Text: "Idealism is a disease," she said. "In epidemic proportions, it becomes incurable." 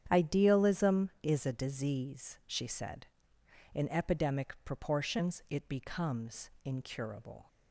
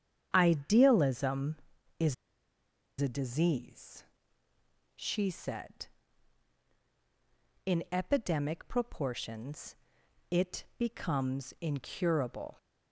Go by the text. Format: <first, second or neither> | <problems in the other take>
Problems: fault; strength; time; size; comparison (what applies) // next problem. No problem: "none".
first | starts louder than the rest; strong; until 1.3 s; 8.5 dB; strong in the first // pauses between "is" and "a"; noticeable; at 2.1 s; 0.86 s long